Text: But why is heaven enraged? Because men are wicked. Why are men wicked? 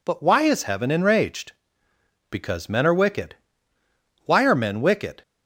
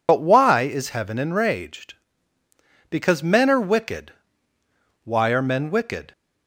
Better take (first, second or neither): first